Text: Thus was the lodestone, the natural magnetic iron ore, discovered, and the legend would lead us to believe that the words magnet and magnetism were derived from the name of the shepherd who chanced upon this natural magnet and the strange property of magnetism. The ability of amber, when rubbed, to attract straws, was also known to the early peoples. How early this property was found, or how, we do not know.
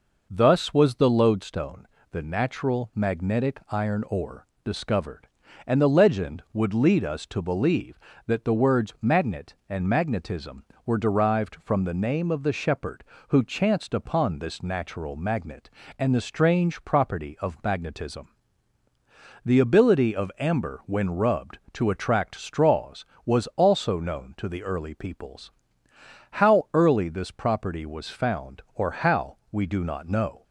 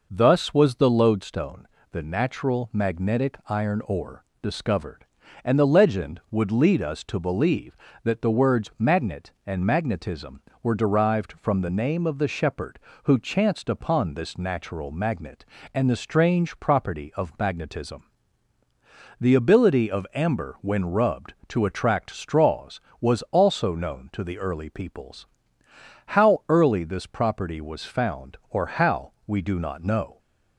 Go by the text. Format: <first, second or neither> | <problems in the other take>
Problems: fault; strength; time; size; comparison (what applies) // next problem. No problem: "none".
neither | none